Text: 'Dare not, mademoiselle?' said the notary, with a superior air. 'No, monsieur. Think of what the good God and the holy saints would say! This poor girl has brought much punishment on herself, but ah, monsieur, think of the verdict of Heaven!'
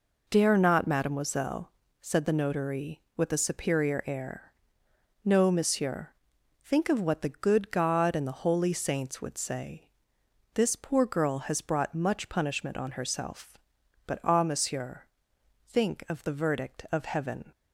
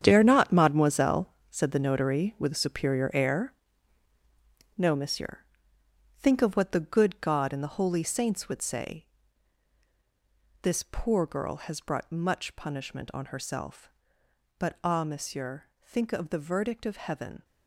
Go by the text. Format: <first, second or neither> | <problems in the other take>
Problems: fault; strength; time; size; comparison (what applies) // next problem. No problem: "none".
first | gets quieter; strong; throughout; 11.5 dB